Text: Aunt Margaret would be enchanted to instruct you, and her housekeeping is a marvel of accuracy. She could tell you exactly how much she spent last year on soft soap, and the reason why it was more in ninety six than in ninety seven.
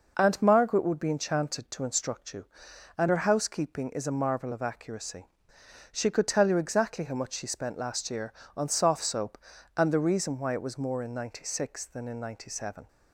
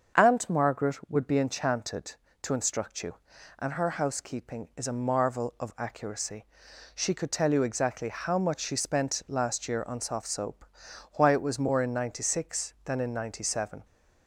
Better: first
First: none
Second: starts louder than the rest; until 1.2 s; 7 dB // skips "and the reason"; at 10.8 s

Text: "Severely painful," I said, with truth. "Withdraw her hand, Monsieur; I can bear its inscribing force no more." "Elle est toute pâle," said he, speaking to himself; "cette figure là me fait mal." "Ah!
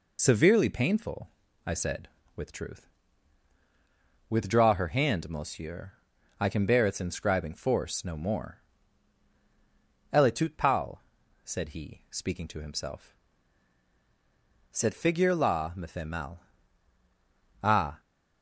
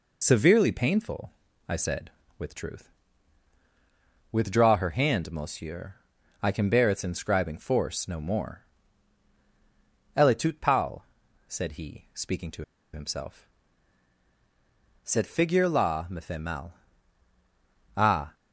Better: first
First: none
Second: pauses between "to" and "himself"; slight; at 12.6 s; 0.30 s long

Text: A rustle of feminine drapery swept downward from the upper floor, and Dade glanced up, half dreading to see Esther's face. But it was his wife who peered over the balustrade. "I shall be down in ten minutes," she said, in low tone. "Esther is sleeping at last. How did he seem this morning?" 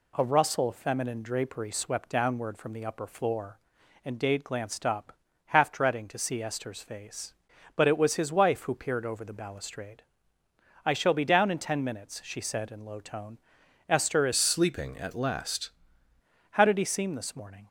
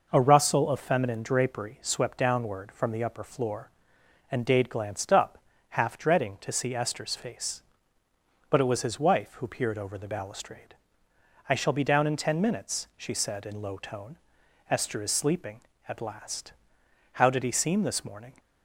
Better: second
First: changes voice from "sleeping" to "last"; from 14.3 to 15.6 s; 1.3 s long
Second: none

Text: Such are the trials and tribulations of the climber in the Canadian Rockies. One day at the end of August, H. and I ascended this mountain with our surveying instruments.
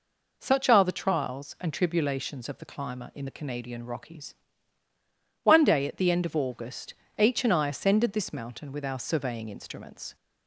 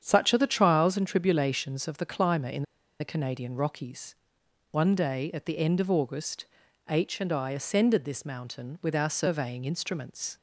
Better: first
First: none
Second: starts louder than the rest; strong; until 1.0 s; 8 dB // pauses between "in" and "the"; at 2.6 s; 0.36 s long

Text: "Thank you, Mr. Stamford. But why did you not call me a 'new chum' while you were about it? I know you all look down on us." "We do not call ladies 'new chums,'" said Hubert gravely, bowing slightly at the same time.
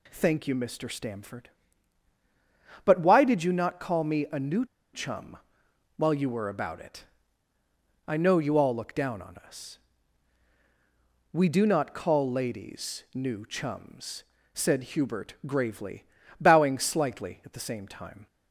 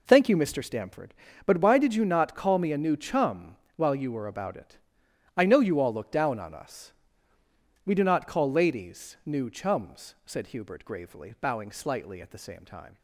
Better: second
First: pauses between "new" and "chum"; slight; at 4.6 s; 0.28 s long // pauses between "chum" and "while"; noticeable; at 5.3 s; 0.62 s long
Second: pauses between "chum" and "while"; slight; at 3.5 s; 0.18 s long

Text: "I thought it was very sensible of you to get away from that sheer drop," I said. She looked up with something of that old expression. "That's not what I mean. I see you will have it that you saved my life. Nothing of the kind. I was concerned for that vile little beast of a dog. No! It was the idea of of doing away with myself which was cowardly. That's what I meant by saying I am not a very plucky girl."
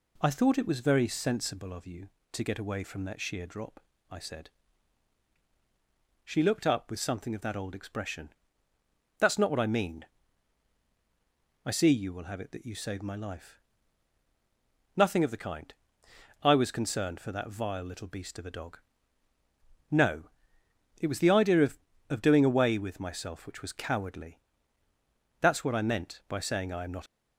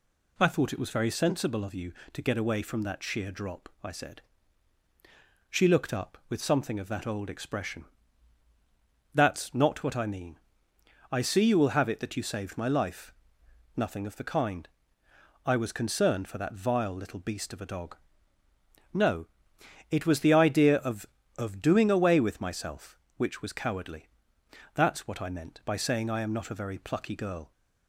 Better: second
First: stops before "a very plucky girl"; at 27.0 s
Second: none

